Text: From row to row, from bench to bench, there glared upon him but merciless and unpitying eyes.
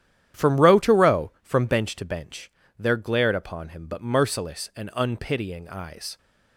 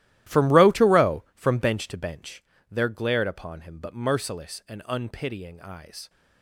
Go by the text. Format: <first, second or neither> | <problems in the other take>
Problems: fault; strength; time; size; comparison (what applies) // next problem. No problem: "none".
first | gets quieter; strong; throughout; 15.5 dB // starts louder than the rest; strong; until 1.4 s; 14.5 dB; strong in the first